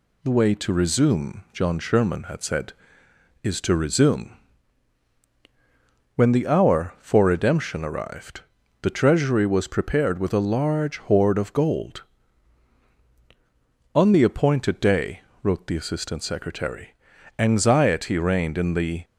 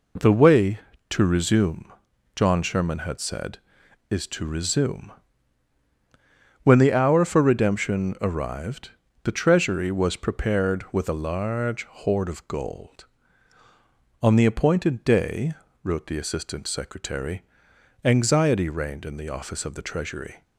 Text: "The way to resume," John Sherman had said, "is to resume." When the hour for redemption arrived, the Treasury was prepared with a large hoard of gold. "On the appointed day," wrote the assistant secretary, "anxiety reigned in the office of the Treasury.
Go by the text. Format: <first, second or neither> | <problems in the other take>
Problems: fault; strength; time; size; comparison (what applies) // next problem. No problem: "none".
second | stops before "office of the Treasury"; at 19.0 s